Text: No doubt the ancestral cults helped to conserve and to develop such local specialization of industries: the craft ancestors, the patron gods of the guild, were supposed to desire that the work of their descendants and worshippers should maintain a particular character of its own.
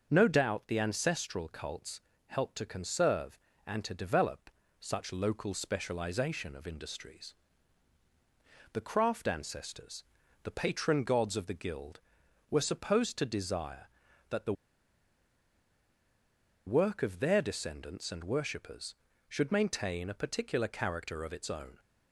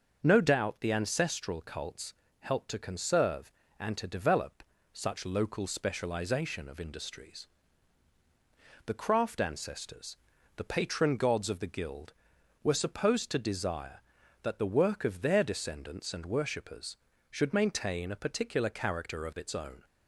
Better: second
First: starts louder than the rest; until 1.1 s; 6.5 dB // pauses between "cults" and "helped"; slight; at 1.9 s; 0.28 s long // pauses between "develop" and "such"; slight; at 4.5 s; 0.28 s long // pauses between "the" and "work"; strong; at 14.5 s; 2.1 s long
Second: starts louder than the rest; until 1.2 s; 6.5 dB // pauses between "cults" and "helped"; slight; at 2.1 s; 0.28 s long // pauses between "develop" and "such"; slight; at 4.6 s; 0.28 s long

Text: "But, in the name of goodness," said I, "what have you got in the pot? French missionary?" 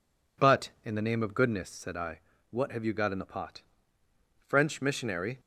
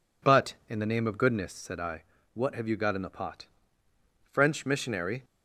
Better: neither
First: none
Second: none

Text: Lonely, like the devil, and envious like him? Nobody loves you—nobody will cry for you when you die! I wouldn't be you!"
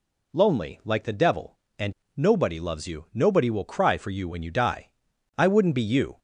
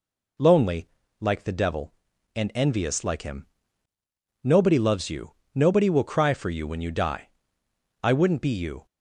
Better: second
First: skips "envious like him"; at 2.0 s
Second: none

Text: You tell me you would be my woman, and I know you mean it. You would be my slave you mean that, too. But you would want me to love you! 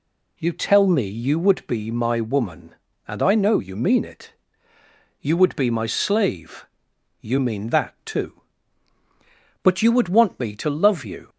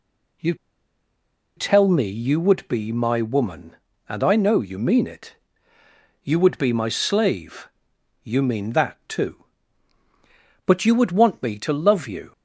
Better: first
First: pauses between "slave" and "you"; noticeable; at 6.6 s; 0.56 s long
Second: pauses between "You" and "tell"; at 0.5 s; 1.0 s long // pauses between "slave" and "you"; noticeable; at 7.6 s; 0.56 s long

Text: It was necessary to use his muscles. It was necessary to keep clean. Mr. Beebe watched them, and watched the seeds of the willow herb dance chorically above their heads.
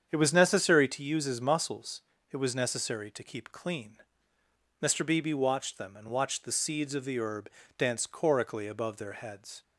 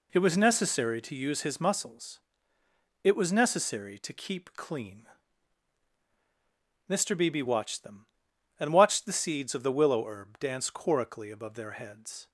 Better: second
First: starts louder than the rest; strong; until 1.1 s; 8 dB // skips "willow"; at 7.1 s // pauses between "herb" and "dance"; slight; at 7.4 s; 0.28 s long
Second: none

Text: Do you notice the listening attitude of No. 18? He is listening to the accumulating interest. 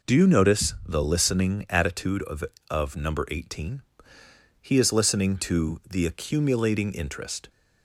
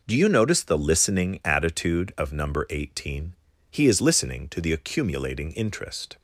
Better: second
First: says "of" twice; at 2.6 s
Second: none

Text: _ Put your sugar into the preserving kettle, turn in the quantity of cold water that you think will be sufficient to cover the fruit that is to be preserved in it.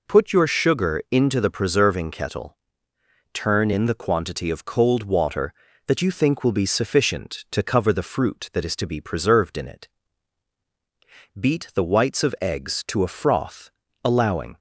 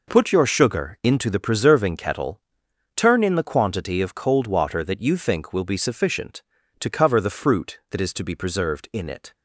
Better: second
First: goes on to say "Beat the whites of eggs to a froth allowing"; strong; from 11.3 s on; 3.1 s long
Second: none

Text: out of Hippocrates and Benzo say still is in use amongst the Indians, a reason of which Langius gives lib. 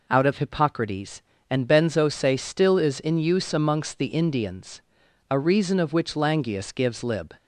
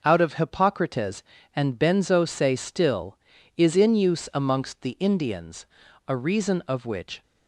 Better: first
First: none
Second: starts louder than the rest; noticeable; until 1.0 s; 6 dB // stops before "Langius gives lib"; at 7.2 s

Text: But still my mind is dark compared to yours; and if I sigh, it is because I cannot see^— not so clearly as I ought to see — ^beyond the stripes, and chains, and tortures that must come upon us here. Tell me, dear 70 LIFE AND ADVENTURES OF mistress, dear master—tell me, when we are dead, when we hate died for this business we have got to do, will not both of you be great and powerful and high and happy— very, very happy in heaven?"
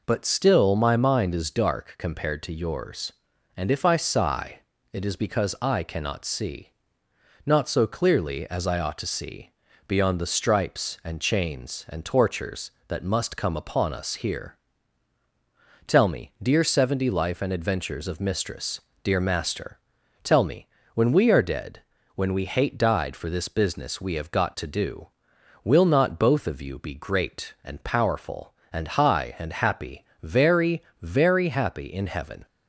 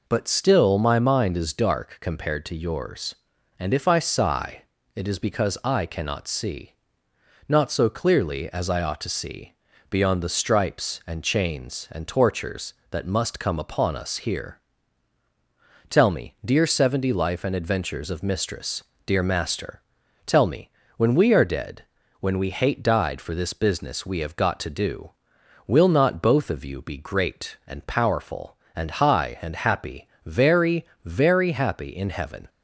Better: neither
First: none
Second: none

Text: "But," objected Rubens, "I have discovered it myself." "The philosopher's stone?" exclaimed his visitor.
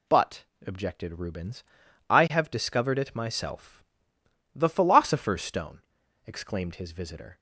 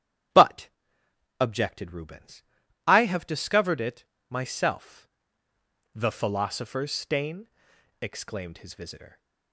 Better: first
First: none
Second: starts louder than the rest; strong; until 2.0 s; 11.5 dB // pauses between "it" and "myself"; slight; at 4.0 s; 0.26 s long // says "stain" for "stone"; at 6.9 s

